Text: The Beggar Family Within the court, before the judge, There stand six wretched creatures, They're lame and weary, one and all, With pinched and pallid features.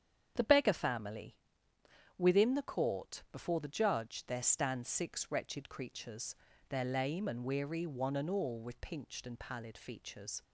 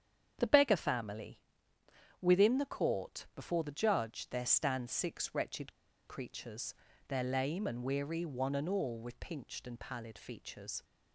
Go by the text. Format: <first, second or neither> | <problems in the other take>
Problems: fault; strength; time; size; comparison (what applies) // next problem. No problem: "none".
first | starts louder than the rest; strong; until 1.3 s; 8.5 dB; strong in the first // pauses between "Family" and "Within"; noticeable; at 1.3 s; 0.82 s long; noticeable in the first // pauses between "wretched" and "creatures"; at 5.7 s; 0.36 s long